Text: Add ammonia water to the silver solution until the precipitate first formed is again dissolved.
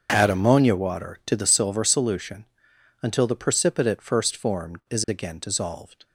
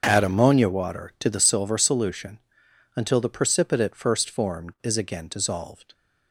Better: neither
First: starts louder than the rest; until 1.1 s; 6.5 dB // pauses between "solution" and "until"; noticeable; at 2.4 s; 0.56 s long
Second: starts louder than the rest; until 1.0 s; 6.5 dB // pauses between "solution" and "until"; noticeable; at 2.3 s; 0.56 s long

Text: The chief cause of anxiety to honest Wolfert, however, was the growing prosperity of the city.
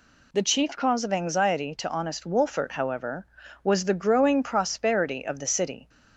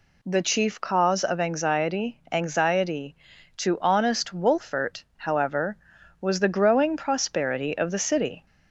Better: first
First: none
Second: says "anxiety" twice; at 2.3 s

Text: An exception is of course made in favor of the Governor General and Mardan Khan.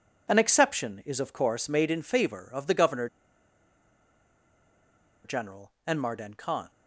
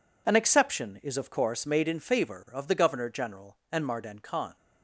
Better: second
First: pauses between "Governor" and "General"; strong; at 3.0 s; 2.1 s long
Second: none

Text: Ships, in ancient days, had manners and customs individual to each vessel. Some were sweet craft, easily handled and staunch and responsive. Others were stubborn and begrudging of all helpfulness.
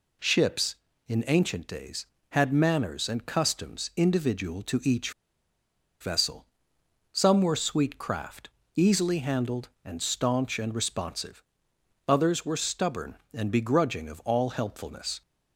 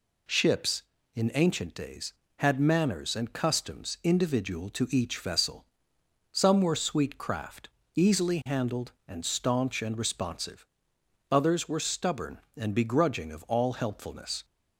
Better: second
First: pauses between "each" and "vessel"; noticeable; at 5.1 s; 0.90 s long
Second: none

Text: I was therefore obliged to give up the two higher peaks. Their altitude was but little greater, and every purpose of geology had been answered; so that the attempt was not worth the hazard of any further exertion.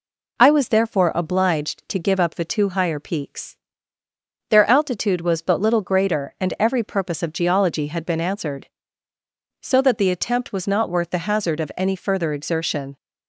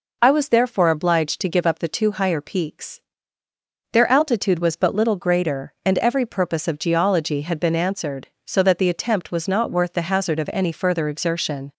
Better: neither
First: none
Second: none

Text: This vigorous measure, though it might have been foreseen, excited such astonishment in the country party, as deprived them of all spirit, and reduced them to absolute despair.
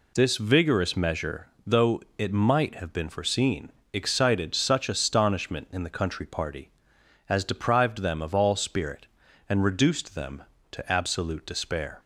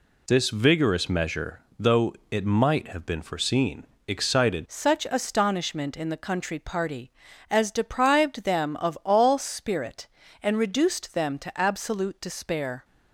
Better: first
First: pauses between "though" and "it"; slight; at 2.0 s; 0.16 s long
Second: pauses between "though" and "it"; slight; at 2.1 s; 0.16 s long // changes voice at "such"; from 4.6 s on; 8.2 s long

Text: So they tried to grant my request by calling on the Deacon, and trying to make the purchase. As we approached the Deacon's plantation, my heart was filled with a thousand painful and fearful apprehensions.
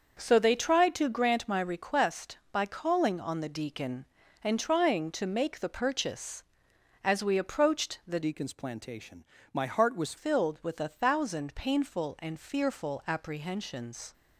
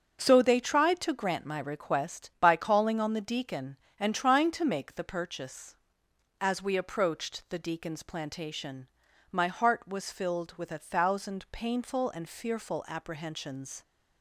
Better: second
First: starts louder than the rest; until 1.2 s; 6.5 dB // changes voice from "Deacon's" to "was"; from 8.2 to 10.1 s; 1.9 s long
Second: starts louder than the rest; strong; until 1.2 s; 7 dB

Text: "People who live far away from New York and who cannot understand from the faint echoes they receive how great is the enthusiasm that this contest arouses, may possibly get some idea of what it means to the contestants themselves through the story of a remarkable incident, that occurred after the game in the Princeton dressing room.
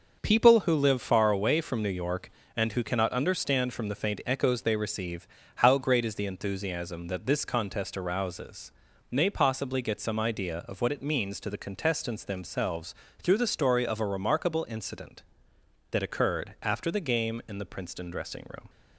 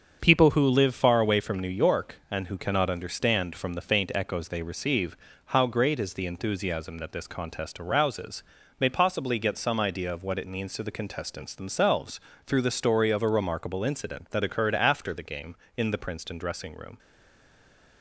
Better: first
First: starts louder than the rest; noticeable; until 1.2 s; 6 dB // pauses between "receive" and "how"; slight; at 5.2 s; 0.30 s long // pauses between "themselves" and "through"; slight; at 12.9 s; 0.28 s long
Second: starts louder than the rest; until 1.2 s; 6.5 dB // pauses between "receive" and "how"; slight; at 5.1 s; 0.30 s long // pauses between "themselves" and "through"; slight; at 12.1 s; 0.30 s long // stays silent after the last word; from 16.9 s on; 1.1 s long

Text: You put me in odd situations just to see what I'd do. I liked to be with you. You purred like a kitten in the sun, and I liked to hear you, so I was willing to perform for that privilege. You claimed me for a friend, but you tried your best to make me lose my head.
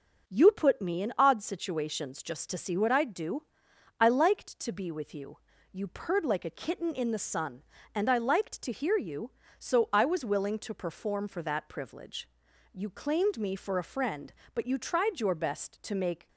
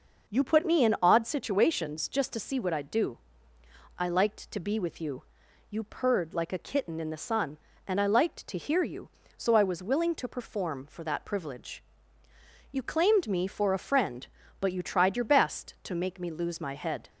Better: second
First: starts louder than the rest; noticeable; until 1.3 s; 6 dB // stops before "me lose my head"; at 16.2 s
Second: none

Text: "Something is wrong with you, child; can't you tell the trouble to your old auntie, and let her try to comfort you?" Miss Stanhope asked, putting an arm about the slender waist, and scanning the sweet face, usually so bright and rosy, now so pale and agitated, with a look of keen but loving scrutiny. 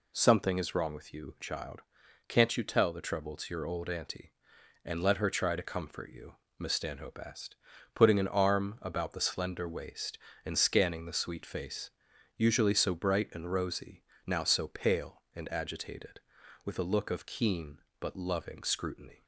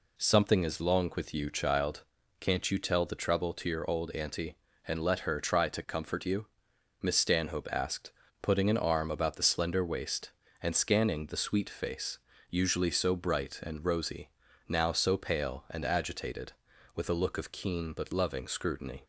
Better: first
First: none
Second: says "long" for "wrong"; at 0.8 s

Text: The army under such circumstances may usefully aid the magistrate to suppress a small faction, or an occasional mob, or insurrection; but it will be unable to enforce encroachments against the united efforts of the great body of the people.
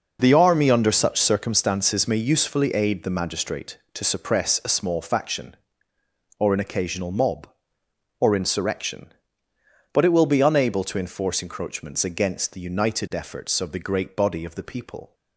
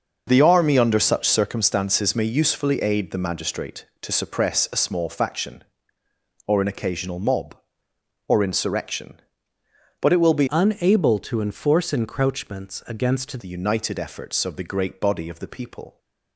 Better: first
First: none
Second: starts louder than the rest; noticeable; until 1.2 s; 6 dB // changes voice from "unable" to "against"; from 10.4 to 13.3 s; 2.9 s long

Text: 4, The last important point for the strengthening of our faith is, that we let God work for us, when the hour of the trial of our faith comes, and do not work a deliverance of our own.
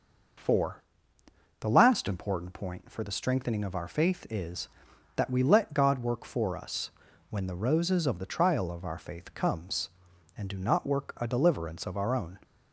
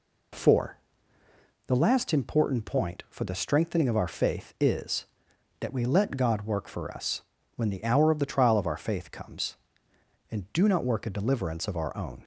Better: second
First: says "roses" for "hour"; at 7.5 s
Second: none

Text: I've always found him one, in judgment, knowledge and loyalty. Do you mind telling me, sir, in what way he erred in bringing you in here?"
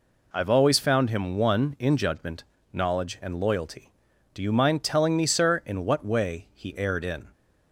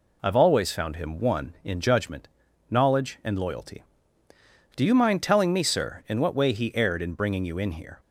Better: second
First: stops before "bringing you in here"; at 7.3 s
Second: none

